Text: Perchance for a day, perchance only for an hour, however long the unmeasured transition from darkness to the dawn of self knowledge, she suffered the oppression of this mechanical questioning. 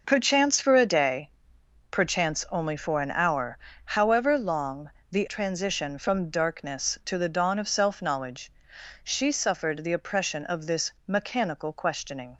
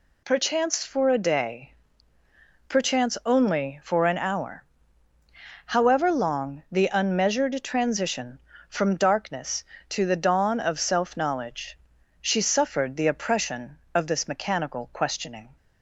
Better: second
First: pauses between "long" and "the"; slight; at 4.9 s; 0.20 s long // skips "unmeasured"; at 5.2 s // pauses between "this" and "mechanical"; slight; at 10.9 s; 0.16 s long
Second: none

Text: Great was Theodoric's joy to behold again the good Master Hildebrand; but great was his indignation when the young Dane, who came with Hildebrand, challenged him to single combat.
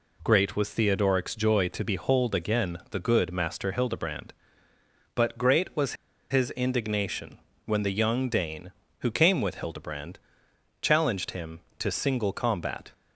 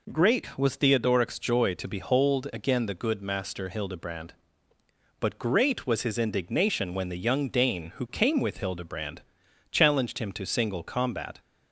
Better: second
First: pauses between "was" and "his"; at 5.9 s; 0.37 s long // pauses between "indignation" and "when"; slight; at 7.3 s; 0.26 s long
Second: none

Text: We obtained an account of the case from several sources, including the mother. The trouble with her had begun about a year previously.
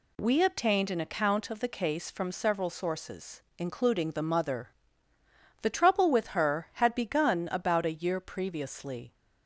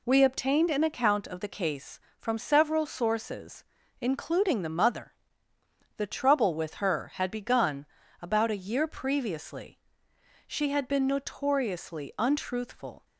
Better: first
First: none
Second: pauses between "begun" and "about"; slight; at 7.8 s; 0.36 s long // goes on to say "She had been notoriously untruthful"; strong; from 10.4 s on; 2.6 s long

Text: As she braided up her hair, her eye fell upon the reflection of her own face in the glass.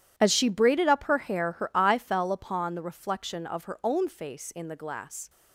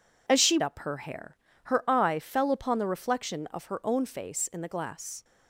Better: first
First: none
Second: skips "braided"; at 0.6 s

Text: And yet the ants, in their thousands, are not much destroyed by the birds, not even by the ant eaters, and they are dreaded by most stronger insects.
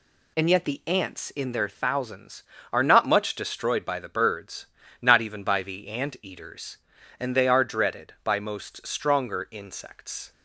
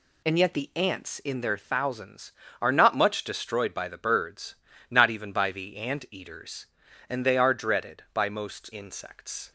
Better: first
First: none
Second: skips "stronger"; at 8.7 s

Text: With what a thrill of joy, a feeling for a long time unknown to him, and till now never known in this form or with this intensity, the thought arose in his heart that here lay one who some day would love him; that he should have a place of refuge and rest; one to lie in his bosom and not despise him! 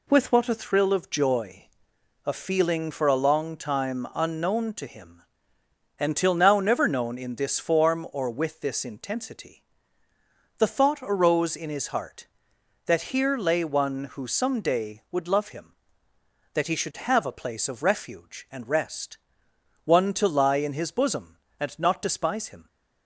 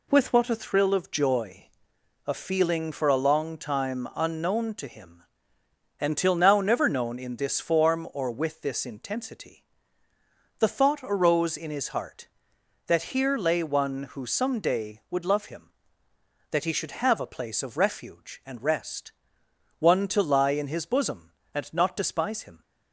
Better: neither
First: none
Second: none

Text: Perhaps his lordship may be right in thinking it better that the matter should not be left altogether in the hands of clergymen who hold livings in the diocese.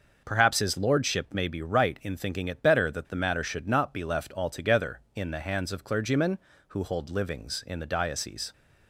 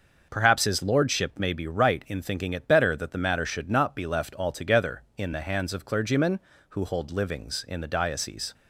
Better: neither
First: none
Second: none

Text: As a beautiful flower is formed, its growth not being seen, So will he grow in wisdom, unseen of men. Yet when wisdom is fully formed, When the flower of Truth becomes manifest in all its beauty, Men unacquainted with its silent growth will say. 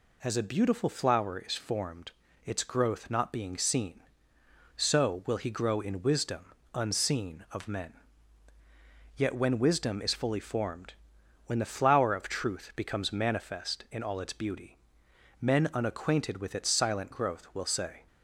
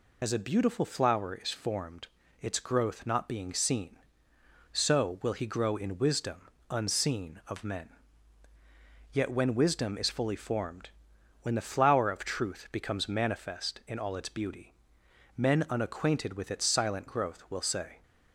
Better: first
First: none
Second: loses the start of "As"; at 0.2 s; 35 ms

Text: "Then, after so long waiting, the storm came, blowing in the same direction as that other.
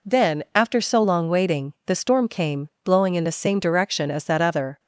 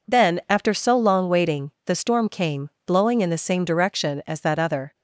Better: neither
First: none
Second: none

